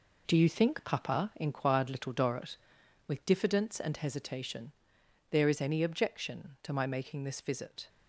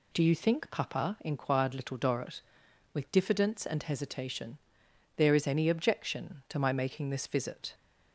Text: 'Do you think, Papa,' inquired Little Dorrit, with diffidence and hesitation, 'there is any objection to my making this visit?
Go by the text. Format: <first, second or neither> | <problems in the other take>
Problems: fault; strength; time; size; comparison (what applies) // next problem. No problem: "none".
second | gets quieter; strong; throughout; 7.5 dB